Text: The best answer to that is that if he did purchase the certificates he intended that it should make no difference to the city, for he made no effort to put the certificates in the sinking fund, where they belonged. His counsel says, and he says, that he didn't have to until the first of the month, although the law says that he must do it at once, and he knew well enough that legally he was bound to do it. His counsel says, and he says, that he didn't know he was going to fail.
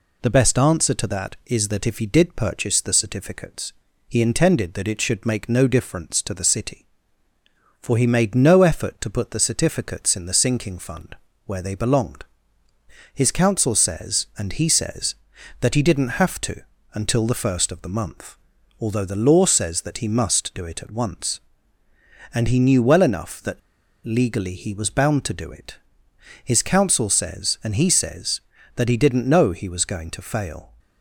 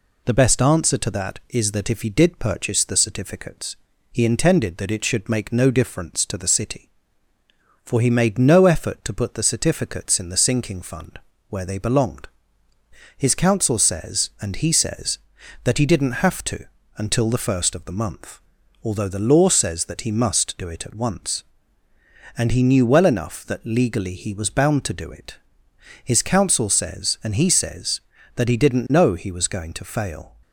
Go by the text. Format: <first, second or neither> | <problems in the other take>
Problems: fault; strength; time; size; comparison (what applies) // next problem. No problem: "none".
second | pauses between "certificates" and "he"; slight; at 3.7 s; 0.36 s long; slight in the second // pauses between "to" and "until"; slight; at 16.6 s; 0.32 s long; slight in the second // pauses between "that" and "legally"; at 23.5 s; 0.45 s long